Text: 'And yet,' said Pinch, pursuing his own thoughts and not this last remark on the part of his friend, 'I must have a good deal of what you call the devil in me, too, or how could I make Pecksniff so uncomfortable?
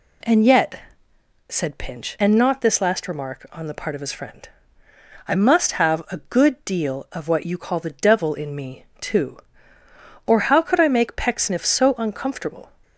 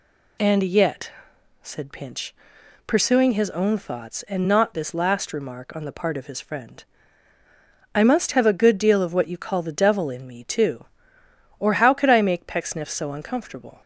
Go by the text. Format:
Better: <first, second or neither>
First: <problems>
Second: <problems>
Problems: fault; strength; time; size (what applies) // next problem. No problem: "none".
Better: second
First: skips "pursuing his own thoughts"; at 2.1 s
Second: none